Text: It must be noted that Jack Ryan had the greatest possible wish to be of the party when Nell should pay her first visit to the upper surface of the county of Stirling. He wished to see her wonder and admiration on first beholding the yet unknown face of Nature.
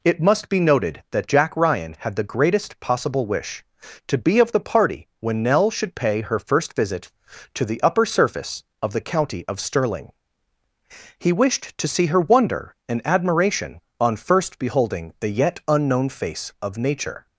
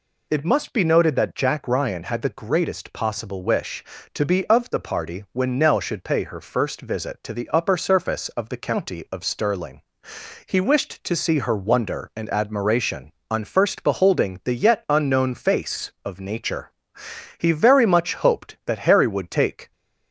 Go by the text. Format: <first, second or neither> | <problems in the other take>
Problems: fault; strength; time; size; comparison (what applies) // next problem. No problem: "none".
first | goes on to say "He very much hoped that Harry would take"; strong; from 17.3 s on; 2.3 s long